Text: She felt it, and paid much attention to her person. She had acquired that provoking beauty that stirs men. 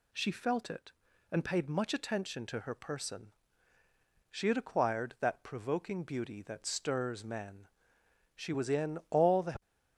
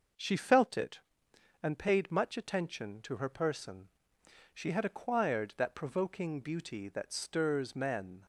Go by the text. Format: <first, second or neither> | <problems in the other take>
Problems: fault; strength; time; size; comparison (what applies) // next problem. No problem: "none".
second | goes on to say "She was in all the"; noticeable; from 8.3 s on; 1.2 s long